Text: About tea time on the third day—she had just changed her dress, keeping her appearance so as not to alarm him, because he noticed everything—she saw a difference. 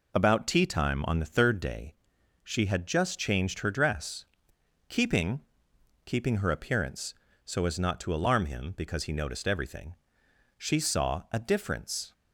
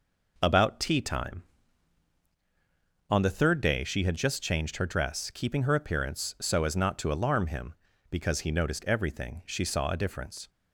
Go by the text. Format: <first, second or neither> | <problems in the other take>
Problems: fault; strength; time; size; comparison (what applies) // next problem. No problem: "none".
second | says "keeping" twice; at 6.0 s